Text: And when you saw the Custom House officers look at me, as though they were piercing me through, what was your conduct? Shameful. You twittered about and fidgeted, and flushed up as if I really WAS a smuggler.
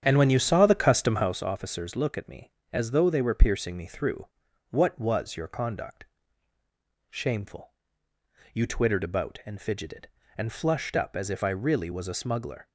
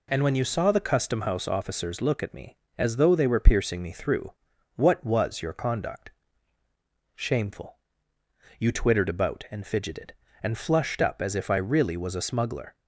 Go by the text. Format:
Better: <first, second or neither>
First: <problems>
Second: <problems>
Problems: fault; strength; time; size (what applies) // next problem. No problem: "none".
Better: second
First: starts louder than the rest; strong; until 1.4 s; 9 dB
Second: none